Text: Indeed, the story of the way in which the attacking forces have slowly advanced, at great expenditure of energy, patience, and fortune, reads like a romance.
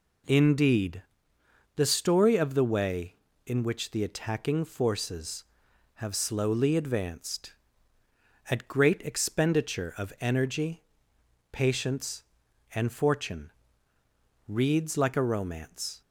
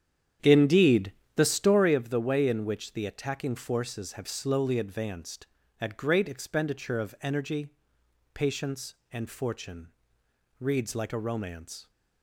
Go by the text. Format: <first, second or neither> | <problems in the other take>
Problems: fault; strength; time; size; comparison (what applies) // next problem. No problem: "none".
first | starts louder than the rest; strong; until 2.0 s; 9 dB